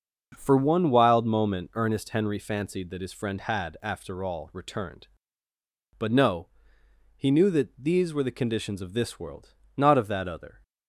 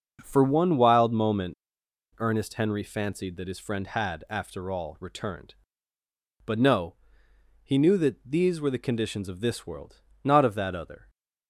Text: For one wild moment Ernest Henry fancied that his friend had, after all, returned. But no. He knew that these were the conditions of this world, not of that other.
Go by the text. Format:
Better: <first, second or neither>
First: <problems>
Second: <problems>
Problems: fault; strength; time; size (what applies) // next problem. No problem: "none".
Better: first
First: starts louder than the rest; until 1.3 s; 6 dB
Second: starts louder than the rest; until 1.2 s; 6 dB // pauses between "moment" and "Ernest"; noticeable; at 1.5 s; 0.63 s long